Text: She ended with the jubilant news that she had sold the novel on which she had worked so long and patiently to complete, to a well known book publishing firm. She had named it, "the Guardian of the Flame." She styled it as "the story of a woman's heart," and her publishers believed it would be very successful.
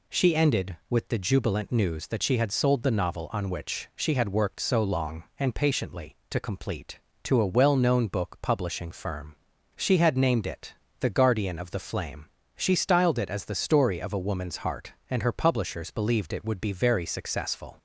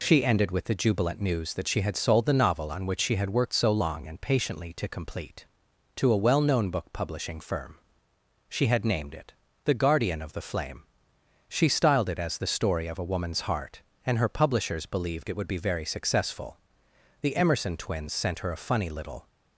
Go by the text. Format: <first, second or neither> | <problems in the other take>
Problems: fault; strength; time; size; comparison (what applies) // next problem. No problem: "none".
first | goes on to say "The Emerson twins sent her a funny little"; strong; from 17.1 s on; 2.0 s long